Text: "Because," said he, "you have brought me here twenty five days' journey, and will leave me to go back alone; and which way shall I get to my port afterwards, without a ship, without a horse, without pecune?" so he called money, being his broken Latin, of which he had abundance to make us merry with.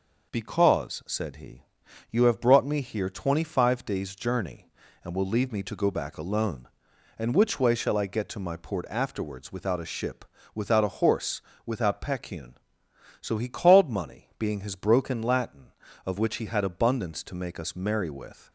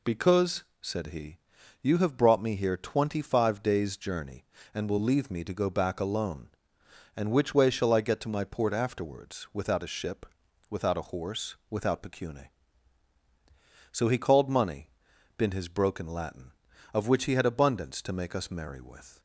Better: first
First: none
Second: says "been" for "being"; at 15.3 s

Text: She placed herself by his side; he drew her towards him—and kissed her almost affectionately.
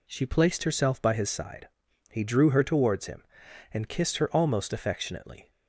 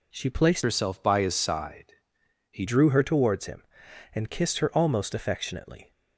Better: first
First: none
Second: changes voice from "herself" to "he"; from 0.6 to 2.6 s; 2.0 s long

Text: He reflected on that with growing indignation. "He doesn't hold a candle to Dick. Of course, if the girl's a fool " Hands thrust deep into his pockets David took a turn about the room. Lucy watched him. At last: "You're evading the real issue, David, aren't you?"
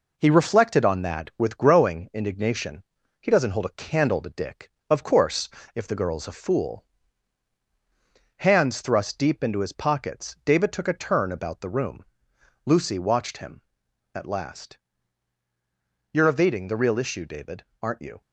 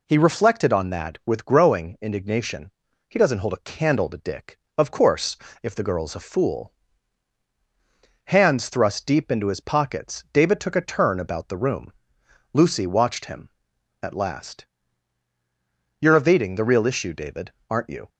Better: second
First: gets quieter; slight; throughout; 3 dB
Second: none

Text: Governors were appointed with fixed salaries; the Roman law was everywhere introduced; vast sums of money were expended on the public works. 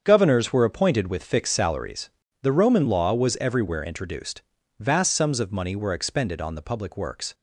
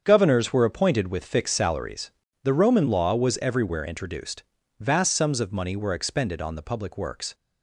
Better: neither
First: starts louder than the rest; strong; until 1.0 s; 7 dB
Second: starts louder than the rest; strong; until 1.0 s; 7.5 dB

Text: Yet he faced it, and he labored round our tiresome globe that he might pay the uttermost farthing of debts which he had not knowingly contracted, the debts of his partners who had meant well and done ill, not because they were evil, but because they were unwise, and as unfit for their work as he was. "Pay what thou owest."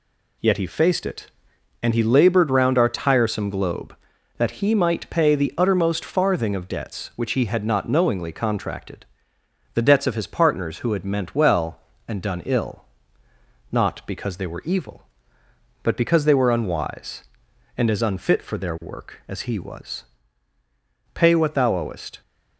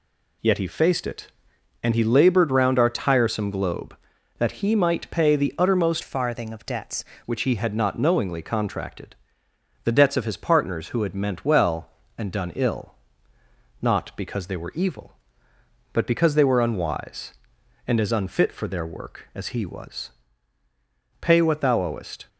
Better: first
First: none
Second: changes voice from "farthing" to "debts"; from 6.0 to 7.0 s; 1.0 s long

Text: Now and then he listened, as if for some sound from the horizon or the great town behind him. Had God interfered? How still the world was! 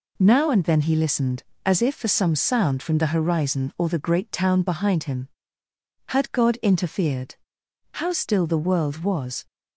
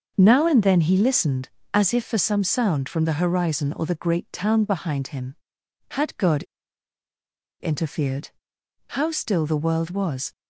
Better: first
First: none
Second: starts louder than the rest; until 1.1 s; 6.5 dB // pauses between "God" and "interfered"; at 6.4 s; 1.1 s long

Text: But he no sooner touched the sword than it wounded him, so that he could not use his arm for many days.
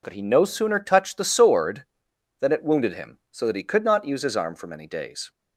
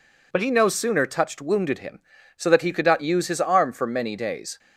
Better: first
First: none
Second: skips "the sword than it"; at 1.4 s

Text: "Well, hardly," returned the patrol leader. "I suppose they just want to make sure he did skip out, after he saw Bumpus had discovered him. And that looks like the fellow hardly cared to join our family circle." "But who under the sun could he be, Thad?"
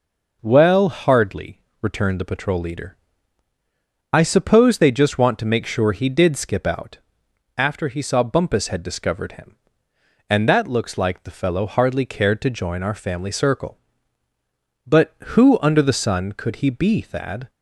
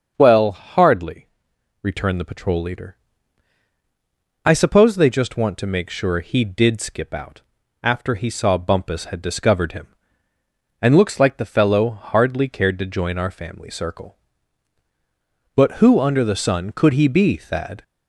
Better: first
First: none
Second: starts louder than the rest; until 1.1 s; 7 dB // skips "that"; at 10.9 s

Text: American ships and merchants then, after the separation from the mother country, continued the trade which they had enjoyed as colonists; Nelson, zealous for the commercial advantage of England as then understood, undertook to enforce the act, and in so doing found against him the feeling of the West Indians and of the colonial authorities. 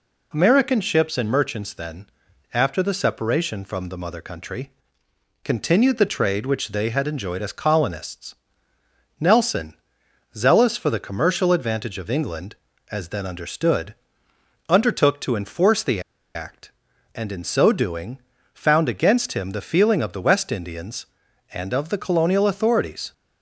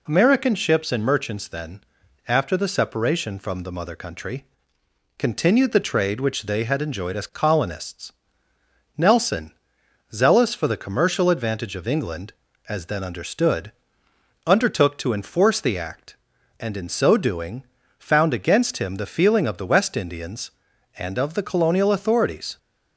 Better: second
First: pauses between "the" and "act"; slight; at 16.0 s; 0.34 s long // pauses between "doing" and "found"; slight; at 18.1 s; 0.34 s long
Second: pauses between "doing" and "found"; slight; at 17.6 s; 0.34 s long

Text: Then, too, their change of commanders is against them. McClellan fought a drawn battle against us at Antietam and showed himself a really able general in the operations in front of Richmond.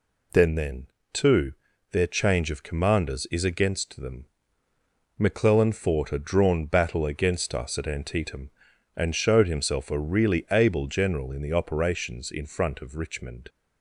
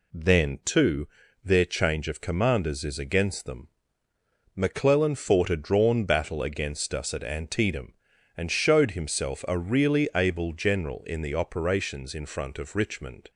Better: second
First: says "Then" twice; at 0.5 s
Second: none

